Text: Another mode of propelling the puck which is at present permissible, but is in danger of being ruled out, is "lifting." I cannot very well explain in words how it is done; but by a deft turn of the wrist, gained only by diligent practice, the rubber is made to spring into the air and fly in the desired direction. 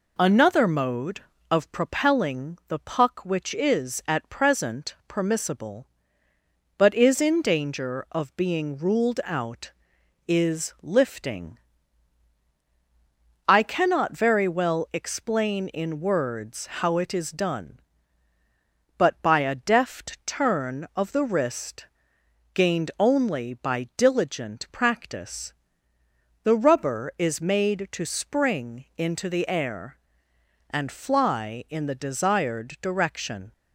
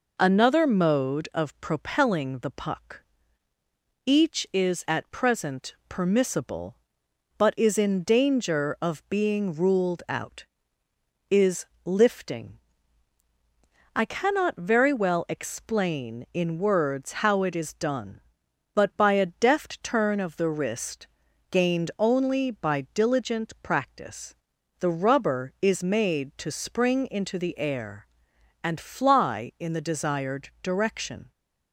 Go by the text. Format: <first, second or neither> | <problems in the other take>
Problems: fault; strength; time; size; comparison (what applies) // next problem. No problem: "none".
first | says "each" for "which"; at 4.0 s // pauses between "present" and "permissible"; slight; at 5.7 s; 0.16 s long // pauses between "is" and "lifting"; slight; at 11.6 s; 0.20 s long